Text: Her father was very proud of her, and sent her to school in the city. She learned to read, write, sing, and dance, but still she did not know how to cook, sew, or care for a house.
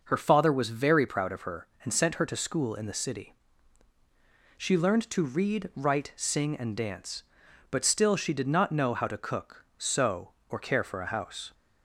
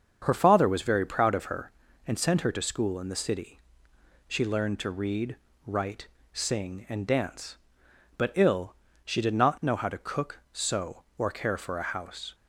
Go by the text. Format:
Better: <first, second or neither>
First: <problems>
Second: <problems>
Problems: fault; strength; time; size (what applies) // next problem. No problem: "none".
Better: first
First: none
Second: starts louder than the rest; until 1.2 s; 7 dB // says "ill" for "still"; at 8.3 s